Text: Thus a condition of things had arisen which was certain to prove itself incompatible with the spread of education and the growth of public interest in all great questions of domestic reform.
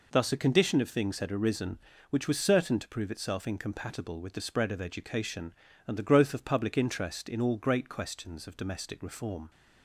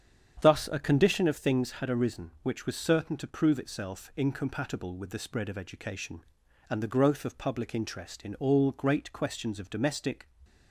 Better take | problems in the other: first | starts louder than the rest; strong; until 1.4 s; 8.5 dB // stops before "reform"; at 10.4 s

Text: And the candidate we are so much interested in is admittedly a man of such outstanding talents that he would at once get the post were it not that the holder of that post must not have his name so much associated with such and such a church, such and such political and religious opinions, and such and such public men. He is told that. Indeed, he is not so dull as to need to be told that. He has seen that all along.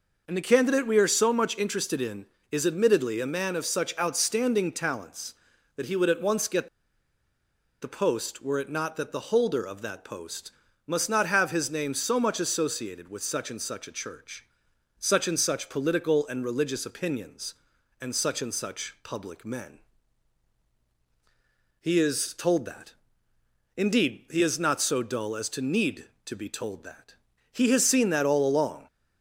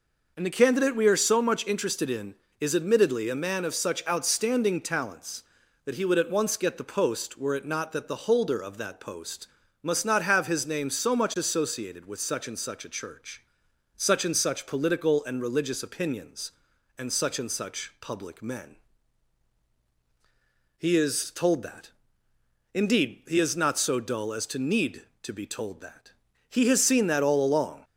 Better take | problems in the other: second | pauses between "get" and "the"; at 6.6 s; 1.1 s long // pauses between "post" and "must"; slight; at 10.5 s; 0.36 s long; slight in the second

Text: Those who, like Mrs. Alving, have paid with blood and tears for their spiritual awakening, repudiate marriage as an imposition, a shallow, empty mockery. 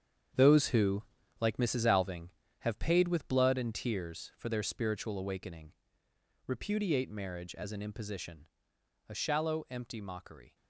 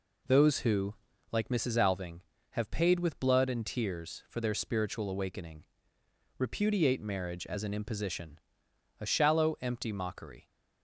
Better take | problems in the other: second | gets quieter; strong; throughout; 10.5 dB

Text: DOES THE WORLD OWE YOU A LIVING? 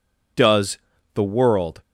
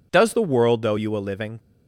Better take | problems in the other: second | pauses between "DOES" and "THE"; slight; at 0.7 s; 0.34 s long // stops before "OWE YOU A LIVING"; at 1.8 s

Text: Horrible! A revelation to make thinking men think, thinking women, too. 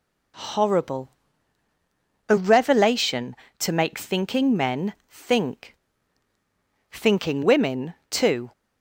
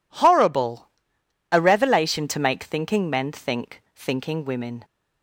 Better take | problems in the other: first | stops before "too"; at 4.8 s

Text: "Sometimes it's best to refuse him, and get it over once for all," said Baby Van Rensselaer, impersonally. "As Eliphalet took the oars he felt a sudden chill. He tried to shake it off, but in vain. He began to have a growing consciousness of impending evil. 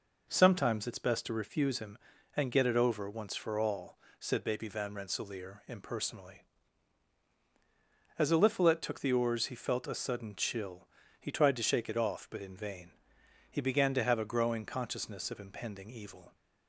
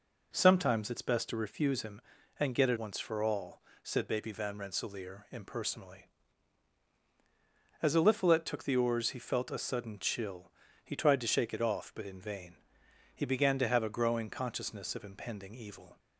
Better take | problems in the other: first | skips "over"; at 2.7 s

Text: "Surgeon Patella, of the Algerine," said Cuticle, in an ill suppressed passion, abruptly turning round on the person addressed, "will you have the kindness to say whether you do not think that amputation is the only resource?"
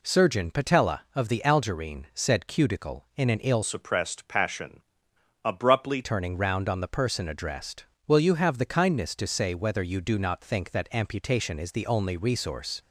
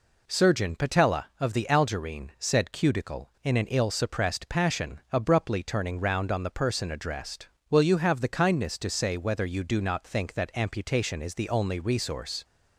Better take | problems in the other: second | changes voice from "suppressed" to "abruptly"; from 3.6 to 6.0 s; 2.4 s long

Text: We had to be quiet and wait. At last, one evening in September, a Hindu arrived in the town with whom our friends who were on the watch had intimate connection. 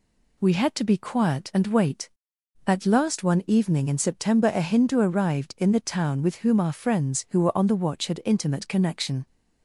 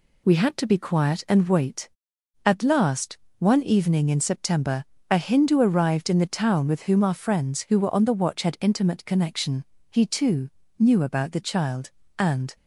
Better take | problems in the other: first | goes on to say "He too knew about the child and"; strong; from 9.9 s on; 2.6 s long

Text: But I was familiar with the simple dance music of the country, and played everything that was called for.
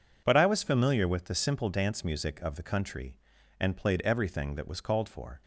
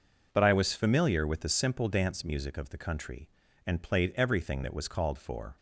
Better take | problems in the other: neither | none

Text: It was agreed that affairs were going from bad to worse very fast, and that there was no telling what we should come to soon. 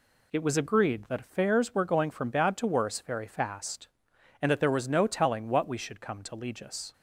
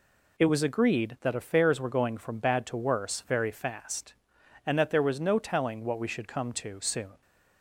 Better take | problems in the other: second | says "legis" for "soon"; at 6.3 s

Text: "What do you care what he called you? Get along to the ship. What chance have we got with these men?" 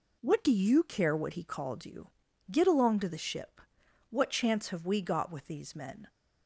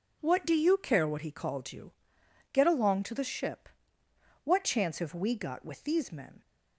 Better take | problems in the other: neither | none

